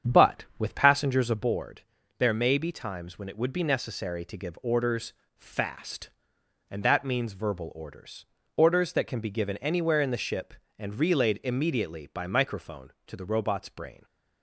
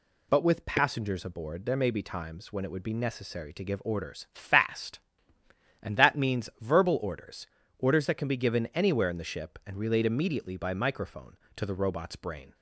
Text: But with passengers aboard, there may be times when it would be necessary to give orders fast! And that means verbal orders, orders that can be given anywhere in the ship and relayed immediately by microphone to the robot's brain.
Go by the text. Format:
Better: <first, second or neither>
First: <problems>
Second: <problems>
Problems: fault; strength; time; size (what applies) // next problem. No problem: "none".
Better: second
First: starts louder than the rest; strong; until 1.6 s; 8 dB // pauses between "orders" and "fast"; slight; at 5.1 s; 0.22 s long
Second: none